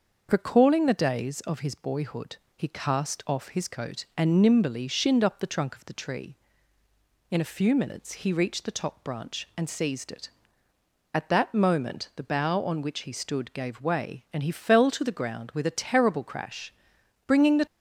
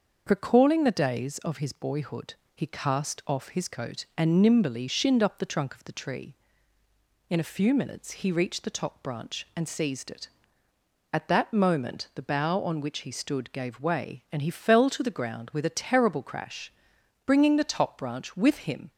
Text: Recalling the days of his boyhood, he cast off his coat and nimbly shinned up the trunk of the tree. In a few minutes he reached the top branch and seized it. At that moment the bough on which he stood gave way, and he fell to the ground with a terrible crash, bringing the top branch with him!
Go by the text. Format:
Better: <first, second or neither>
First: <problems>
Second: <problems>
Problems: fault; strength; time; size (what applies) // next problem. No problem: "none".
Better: second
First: starts louder than the rest; until 1.3 s; 6.5 dB // stops before "top branch with him"; at 17.6 s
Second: starts louder than the rest; until 1.2 s; 6.5 dB